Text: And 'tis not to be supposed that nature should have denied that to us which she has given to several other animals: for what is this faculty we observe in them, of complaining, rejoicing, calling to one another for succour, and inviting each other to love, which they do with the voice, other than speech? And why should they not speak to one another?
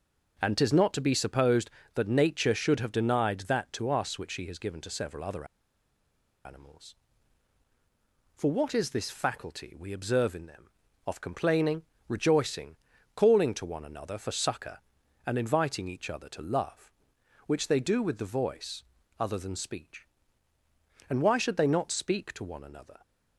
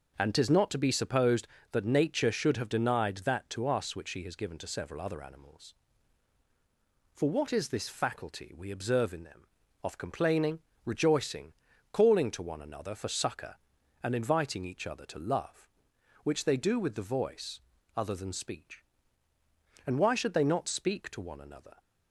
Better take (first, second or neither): second